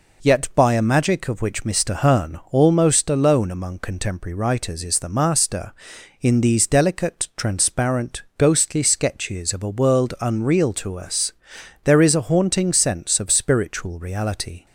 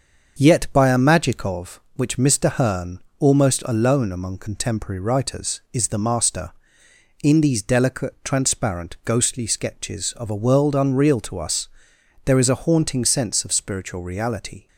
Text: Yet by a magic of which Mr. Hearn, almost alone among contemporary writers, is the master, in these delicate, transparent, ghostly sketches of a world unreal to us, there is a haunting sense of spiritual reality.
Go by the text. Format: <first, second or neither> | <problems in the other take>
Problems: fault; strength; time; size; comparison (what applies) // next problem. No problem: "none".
first | starts louder than the rest; until 1.6 s; 6.5 dB